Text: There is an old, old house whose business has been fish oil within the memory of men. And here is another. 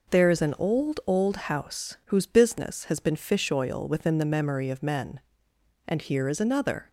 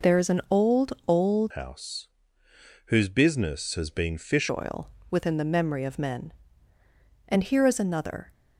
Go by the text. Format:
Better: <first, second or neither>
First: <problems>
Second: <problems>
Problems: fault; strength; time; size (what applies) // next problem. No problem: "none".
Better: first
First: none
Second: changes voice from "house" to "fish"; from 1.5 to 4.5 s; 3.0 s long // pauses between "house" and "whose"; noticeable; at 2.0 s; 0.80 s long // pauses between "oil" and "within"; slight; at 4.8 s; 0.22 s long